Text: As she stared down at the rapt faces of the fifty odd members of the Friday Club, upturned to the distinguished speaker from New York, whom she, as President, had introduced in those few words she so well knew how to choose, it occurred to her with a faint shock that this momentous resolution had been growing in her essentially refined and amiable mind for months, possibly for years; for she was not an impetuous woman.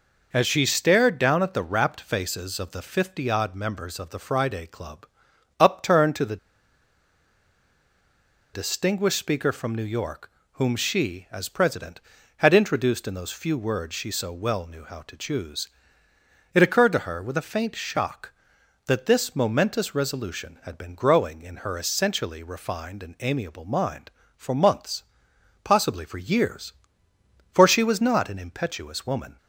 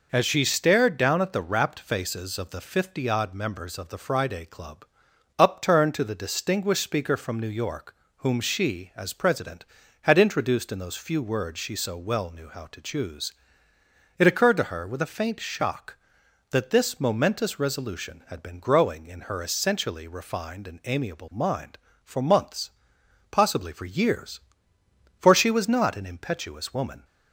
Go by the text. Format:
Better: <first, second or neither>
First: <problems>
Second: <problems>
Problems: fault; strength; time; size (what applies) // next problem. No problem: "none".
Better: second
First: pauses between "the" and "distinguished"; strong; at 6.3 s; 2.1 s long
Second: none